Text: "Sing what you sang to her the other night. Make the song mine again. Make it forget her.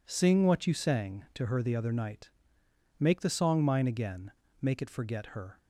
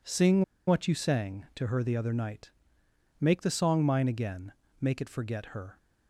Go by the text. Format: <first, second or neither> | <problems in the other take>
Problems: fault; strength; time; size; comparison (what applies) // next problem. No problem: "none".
first | pauses between "Sing" and "what"; slight; at 0.4 s; 0.25 s long